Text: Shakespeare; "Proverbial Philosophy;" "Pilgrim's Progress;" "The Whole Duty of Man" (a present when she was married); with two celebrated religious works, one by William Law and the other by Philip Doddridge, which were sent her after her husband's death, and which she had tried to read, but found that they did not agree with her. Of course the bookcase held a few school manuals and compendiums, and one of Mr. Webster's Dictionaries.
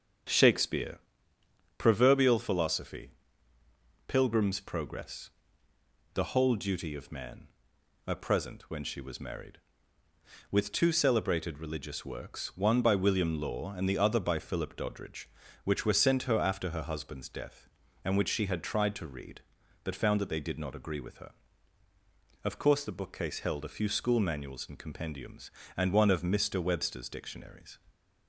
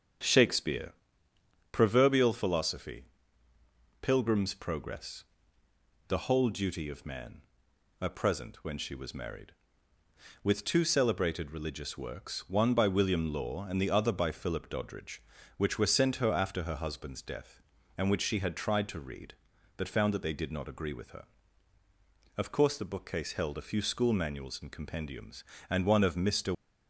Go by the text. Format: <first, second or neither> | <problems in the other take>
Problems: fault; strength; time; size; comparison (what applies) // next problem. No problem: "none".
first | starts louder than the rest; strong; until 2.0 s; 7.5 dB; strong in the first // stops before "Webster's Dictionaries"; at 26.5 s